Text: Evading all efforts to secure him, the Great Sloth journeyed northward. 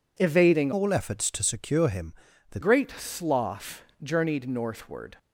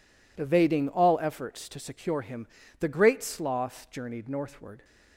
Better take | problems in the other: second | changes voice from "all" to "the"; from 0.7 to 2.5 s; 1.8 s long // pauses between "Sloth" and "journeyed"; slight; at 3.8 s; 0.20 s long

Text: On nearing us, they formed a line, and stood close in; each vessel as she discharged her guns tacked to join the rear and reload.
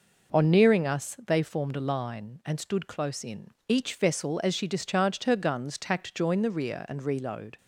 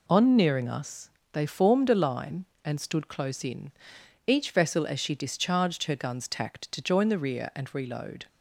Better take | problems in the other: second | skips "to"; at 6.1 s

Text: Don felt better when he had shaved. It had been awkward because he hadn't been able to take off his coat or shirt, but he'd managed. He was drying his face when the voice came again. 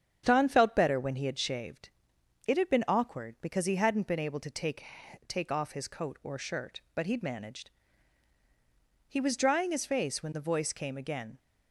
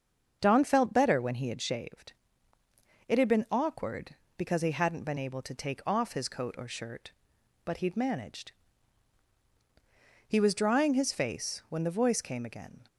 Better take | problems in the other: second | starts louder than the rest; strong; until 1.2 s; 8 dB; also in the second // says "take" twice; at 5.2 s

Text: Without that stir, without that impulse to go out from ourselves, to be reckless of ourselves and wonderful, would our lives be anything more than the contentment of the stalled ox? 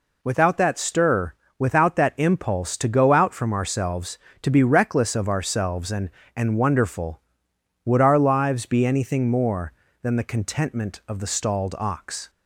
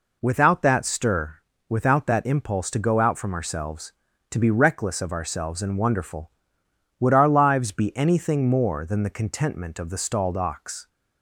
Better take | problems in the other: second | says "and" twice; at 6.3 s

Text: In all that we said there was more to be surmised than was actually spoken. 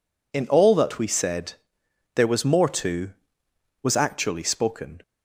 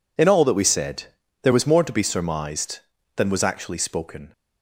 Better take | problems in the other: second | pauses between "said" and "there"; noticeable; at 1.5 s; 0.62 s long; also in the second // skips "be surmised than"; at 3.4 s

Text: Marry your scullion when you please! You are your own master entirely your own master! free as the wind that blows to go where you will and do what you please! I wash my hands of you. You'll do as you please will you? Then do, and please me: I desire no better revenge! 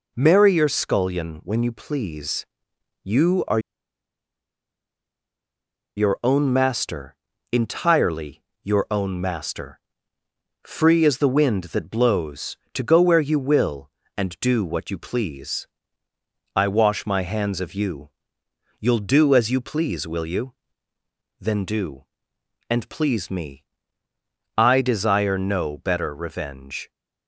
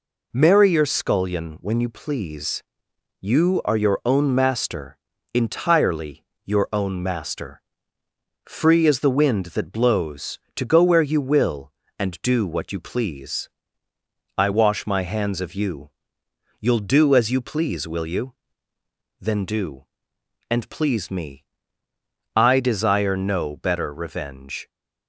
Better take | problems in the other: second | pauses between "are" and "your"; strong; at 3.5 s; 2.3 s long // pauses between "master" and "entirely"; at 7.1 s; 0.38 s long; also in the second // pauses between "entirely" and "your"; slight; at 8.4 s; 0.20 s long; slight in the second

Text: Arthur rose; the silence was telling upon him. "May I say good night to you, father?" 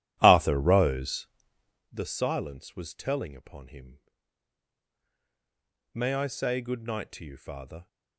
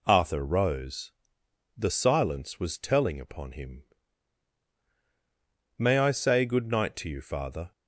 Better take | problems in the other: second | starts louder than the rest; strong; until 2.0 s; 12.5 dB

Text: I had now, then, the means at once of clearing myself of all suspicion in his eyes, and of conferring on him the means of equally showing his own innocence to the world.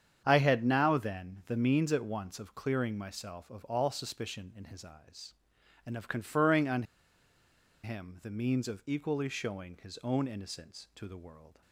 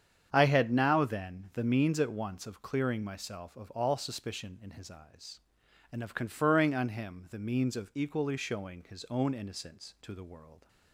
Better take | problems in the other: second | starts louder than the rest; strong; until 1.2 s; 8 dB; strong in the second // pauses between "on" and "him"; at 6.8 s; 1.0 s long

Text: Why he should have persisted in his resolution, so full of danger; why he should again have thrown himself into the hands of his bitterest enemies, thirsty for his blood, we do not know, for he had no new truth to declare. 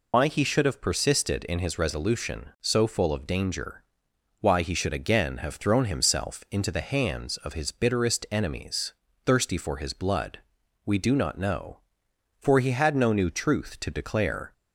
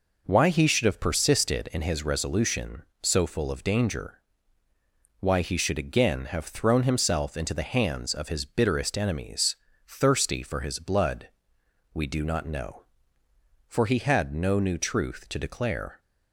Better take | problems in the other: second | loses the start of "Why"; at 0.1 s; 75 ms

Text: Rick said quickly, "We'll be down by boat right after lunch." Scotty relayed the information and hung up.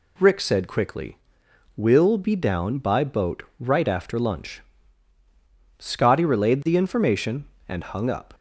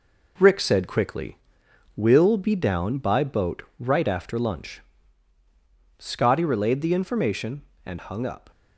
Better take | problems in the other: first | gets quieter; noticeable; throughout; 5.5 dB // pauses between "boat" and "right"; slight; at 3.6 s; 0.16 s long; slight in the first

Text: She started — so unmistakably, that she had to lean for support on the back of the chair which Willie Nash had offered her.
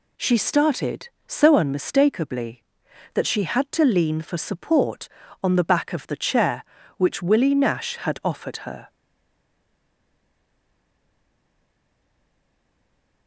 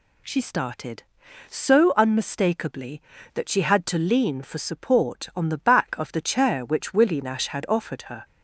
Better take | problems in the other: second | stays silent after the last word; strong; from 8.8 s on; 4.4 s long

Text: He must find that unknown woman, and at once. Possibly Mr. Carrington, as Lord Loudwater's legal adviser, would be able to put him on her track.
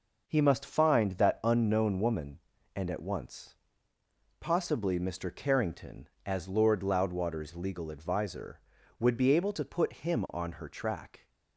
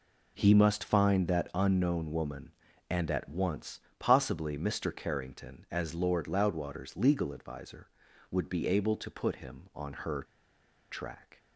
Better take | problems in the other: first | pauses between "her" and "track"; noticeable; at 10.2 s; 0.68 s long

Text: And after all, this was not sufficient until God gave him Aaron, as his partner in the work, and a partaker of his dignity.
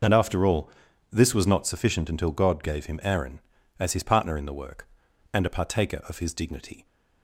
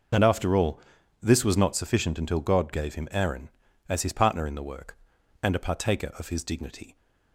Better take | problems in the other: neither | none

